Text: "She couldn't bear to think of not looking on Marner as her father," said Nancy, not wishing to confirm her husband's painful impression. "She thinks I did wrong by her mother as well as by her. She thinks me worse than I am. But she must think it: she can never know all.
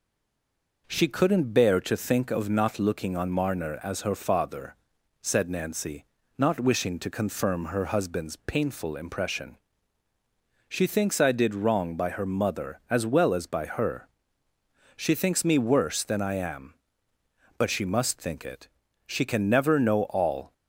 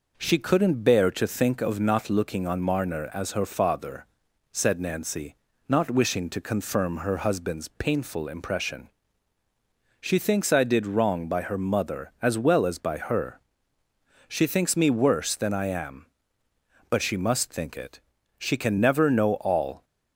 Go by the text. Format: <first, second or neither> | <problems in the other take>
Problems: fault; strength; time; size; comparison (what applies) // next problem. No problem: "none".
second | stays silent before the first word; slight; until 0.8 s; 0.8 s long